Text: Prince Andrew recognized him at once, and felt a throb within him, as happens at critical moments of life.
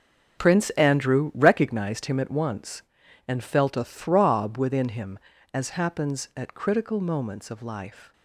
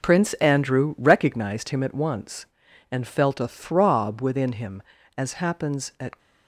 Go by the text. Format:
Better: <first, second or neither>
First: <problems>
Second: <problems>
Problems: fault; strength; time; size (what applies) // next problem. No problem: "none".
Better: first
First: none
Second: stops before "critical moments of life"; at 6.1 s